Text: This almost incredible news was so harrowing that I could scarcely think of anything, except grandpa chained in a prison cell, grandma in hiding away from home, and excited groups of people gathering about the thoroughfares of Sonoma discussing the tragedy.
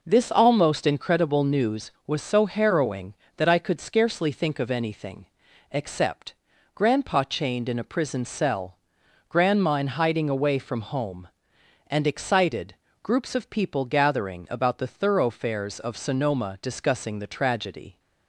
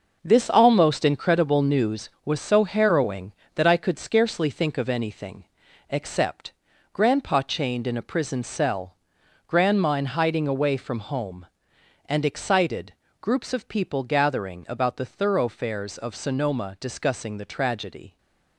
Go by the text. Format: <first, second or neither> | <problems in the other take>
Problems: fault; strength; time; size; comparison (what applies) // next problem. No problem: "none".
first | gets quieter; strong; throughout; 8 dB // pauses between "except" and "grandpa"; at 6.5 s; 0.40 s long; also in the first // pauses between "excited" and "groups"; slight; at 12.9 s; 0.30 s long; slight in the first